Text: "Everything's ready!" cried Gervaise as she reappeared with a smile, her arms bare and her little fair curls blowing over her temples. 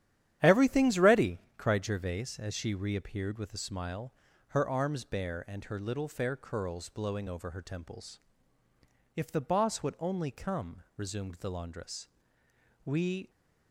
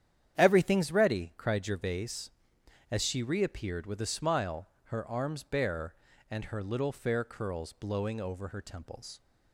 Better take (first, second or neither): second